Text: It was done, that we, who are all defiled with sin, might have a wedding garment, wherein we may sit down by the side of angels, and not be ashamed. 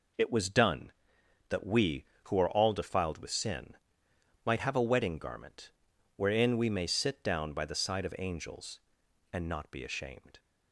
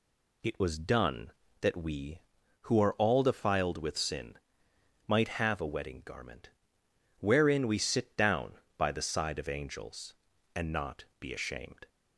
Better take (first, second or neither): first